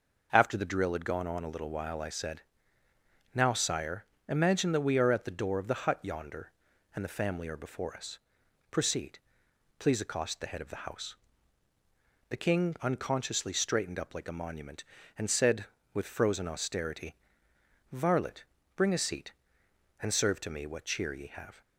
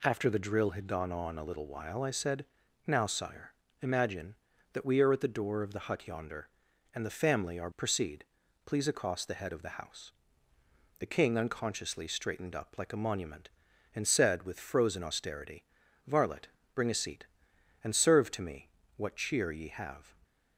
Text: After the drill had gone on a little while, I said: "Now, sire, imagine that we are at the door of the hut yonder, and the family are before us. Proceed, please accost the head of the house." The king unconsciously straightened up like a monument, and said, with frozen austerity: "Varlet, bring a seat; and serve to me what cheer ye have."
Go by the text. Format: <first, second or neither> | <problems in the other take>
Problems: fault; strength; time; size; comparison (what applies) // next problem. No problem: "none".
first | skips "before us"; at 7.7 s // pauses between "me" and "what"; slight; at 18.6 s; 0.26 s long